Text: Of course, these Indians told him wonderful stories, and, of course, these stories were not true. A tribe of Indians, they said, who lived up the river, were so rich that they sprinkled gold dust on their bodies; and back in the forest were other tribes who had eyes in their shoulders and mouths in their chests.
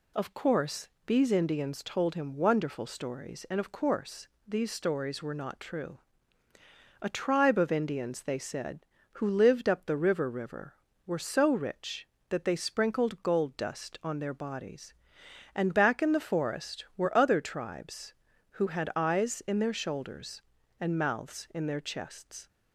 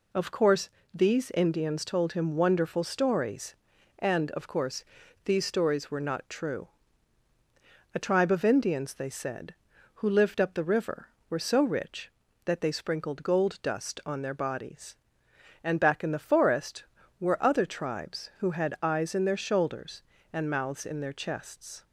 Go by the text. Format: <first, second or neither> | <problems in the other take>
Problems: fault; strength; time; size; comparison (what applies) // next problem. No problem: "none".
second | says "river" twice; at 10.2 s